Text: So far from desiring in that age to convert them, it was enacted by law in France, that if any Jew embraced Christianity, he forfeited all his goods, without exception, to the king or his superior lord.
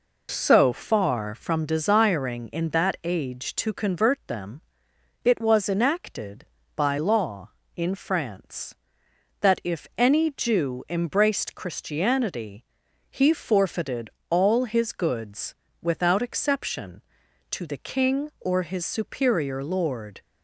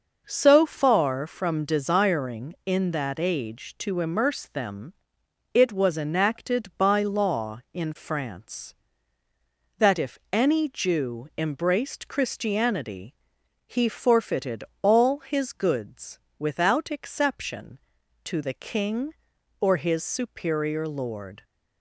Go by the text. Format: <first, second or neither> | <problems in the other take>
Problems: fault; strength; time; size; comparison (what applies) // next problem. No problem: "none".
first | says "immerse" for "convert"; at 3.9 s // pauses between "if" and "any"; slight; at 10.1 s; 0.16 s long // pauses between "forfeited" and "all"; slight; at 14.6 s; 0.18 s long; slight in the first